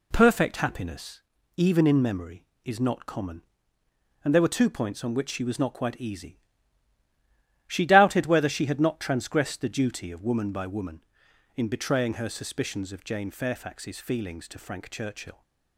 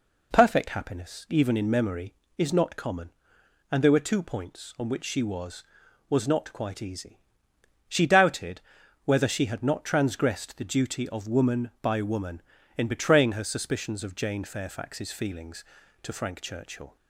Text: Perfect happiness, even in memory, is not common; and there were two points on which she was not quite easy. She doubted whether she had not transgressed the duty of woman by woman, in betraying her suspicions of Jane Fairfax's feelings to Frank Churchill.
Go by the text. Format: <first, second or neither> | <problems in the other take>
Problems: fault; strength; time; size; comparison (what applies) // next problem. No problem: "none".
first | says "was" twice; at 6.0 s // pauses between "doubted" and "whether"; at 8.6 s; 0.42 s long